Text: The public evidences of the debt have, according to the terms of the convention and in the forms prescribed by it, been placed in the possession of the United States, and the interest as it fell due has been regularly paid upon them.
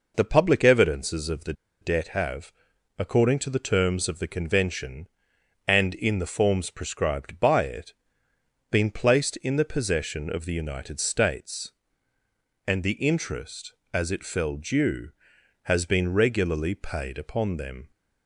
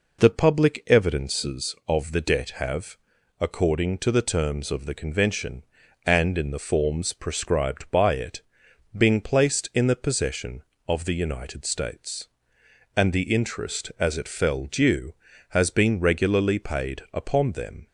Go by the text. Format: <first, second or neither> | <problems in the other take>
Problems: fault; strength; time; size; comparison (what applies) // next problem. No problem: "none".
second | pauses between "the" and "debt"; slight; at 1.5 s; 0.29 s long